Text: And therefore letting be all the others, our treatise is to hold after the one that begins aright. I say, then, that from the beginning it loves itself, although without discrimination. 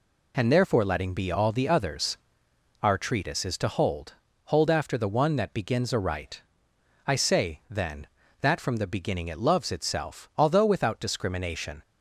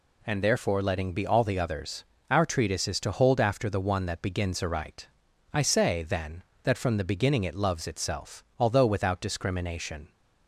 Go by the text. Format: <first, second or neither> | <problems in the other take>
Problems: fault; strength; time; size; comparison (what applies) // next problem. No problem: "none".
second | says "hold" twice; at 4.4 s